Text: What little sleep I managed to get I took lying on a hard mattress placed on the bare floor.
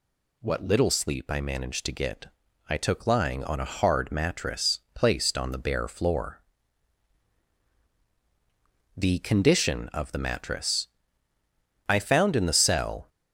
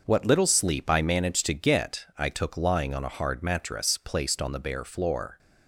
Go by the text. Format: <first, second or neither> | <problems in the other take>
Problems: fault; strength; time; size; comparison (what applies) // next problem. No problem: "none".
second | pauses between "get" and "I"; at 2.2 s; 0.40 s long // pauses between "mattress" and "placed"; slight; at 4.7 s; 0.16 s long // goes on to say "The condition of the mattress I found in the cell"; strong; from 8.9 s on; 4.1 s long